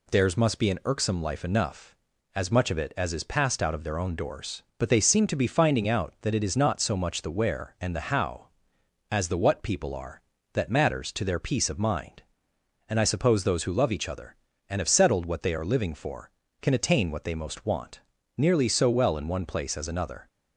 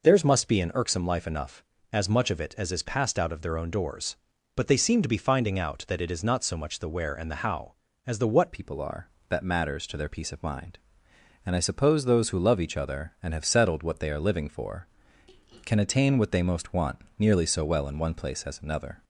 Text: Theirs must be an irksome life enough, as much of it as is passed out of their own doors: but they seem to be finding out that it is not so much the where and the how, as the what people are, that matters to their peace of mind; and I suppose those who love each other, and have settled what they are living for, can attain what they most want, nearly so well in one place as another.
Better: first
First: none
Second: changes voice at "people"; from 8.5 s on; 10.5 s long

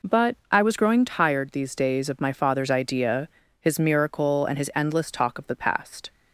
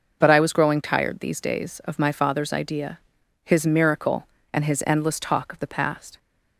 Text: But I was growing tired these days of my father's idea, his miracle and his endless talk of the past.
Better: neither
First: none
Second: none

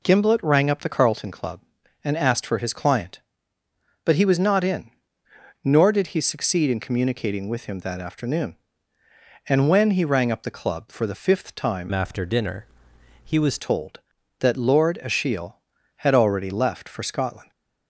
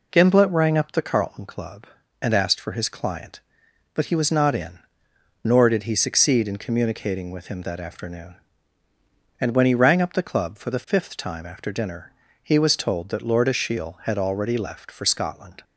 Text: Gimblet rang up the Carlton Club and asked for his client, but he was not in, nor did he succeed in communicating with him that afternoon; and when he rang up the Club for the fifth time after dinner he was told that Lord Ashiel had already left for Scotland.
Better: second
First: changes voice from "after" to "was"; from 11.9 to 13.5 s; 1.6 s long // pauses between "dinner" and "he"; noticeable; at 12.6 s; 0.62 s long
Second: pauses between "dinner" and "he"; slight; at 12.1 s; 0.32 s long

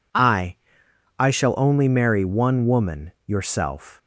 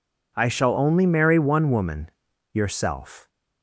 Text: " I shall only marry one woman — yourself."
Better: second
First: says "I" twice; at 1.1 s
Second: none

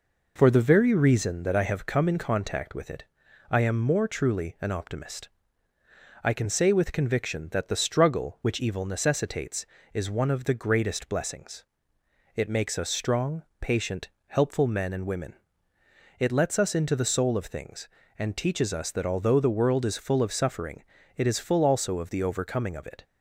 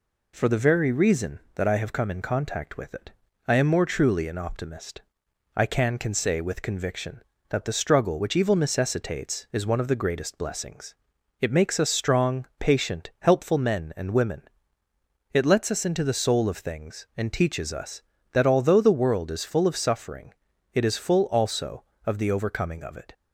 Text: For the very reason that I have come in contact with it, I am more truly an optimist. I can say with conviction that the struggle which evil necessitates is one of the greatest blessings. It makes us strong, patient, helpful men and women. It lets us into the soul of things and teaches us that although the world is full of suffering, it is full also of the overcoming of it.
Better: first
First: none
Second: says "can" twice; at 5.9 s

